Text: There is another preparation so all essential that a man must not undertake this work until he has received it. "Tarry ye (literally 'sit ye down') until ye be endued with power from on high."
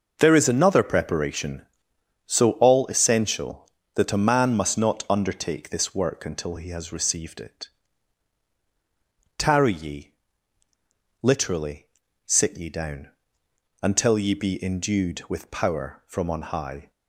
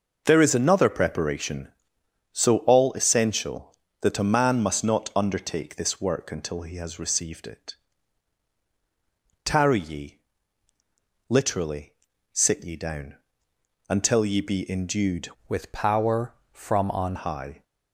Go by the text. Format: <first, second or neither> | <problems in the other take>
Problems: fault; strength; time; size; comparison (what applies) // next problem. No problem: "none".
first | pauses between "literally" and "sit"; at 11.9 s; 0.40 s long; also in the first // changes voice from "with" to "on"; from 15.4 to 17.1 s; 1.7 s long